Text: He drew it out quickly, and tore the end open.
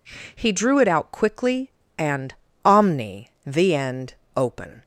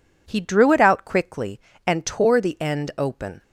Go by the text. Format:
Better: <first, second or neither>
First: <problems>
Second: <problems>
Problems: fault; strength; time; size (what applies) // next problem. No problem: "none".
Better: second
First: says "omni" for "tore"; at 2.6 s // pauses between "end" and "open"; slight; at 4.1 s; 0.22 s long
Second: none